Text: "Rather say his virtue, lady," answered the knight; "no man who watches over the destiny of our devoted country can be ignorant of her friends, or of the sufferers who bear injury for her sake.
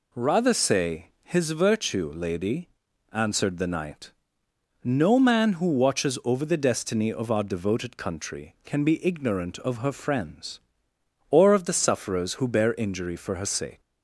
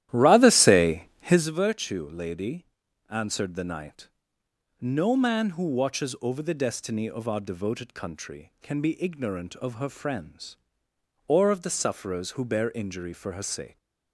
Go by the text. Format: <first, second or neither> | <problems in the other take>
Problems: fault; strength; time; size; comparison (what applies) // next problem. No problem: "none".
first | starts louder than the rest; strong; until 1.6 s; 13 dB // pauses between "say" and "his"; slight; at 1.0 s; 0.18 s long; slight in the first